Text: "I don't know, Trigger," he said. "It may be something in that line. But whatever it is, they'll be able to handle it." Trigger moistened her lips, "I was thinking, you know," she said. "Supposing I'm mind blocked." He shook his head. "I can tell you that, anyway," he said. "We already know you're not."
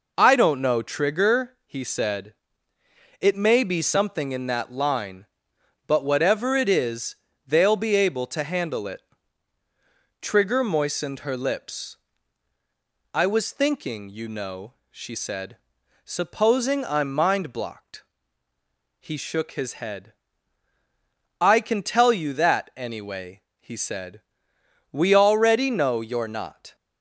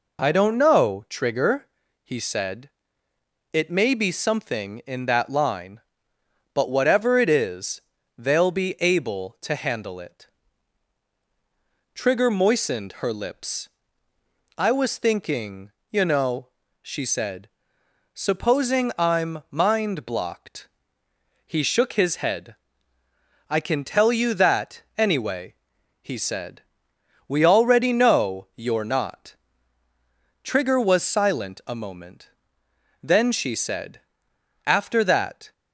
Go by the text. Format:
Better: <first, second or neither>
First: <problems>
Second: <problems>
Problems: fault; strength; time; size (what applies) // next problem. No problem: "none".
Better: first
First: none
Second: goes on to say "Trigger was silent a moment Then she said After that"; strong; from 30.4 s on; 5.1 s long